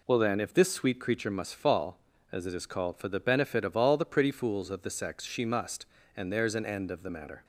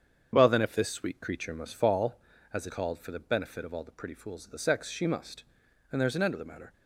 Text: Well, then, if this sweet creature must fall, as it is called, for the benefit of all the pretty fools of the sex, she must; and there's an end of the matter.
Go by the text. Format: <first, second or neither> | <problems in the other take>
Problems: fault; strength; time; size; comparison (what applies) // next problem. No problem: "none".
first | starts louder than the rest; strong; until 1.3 s; 7.5 dB // skips "is"; at 2.7 s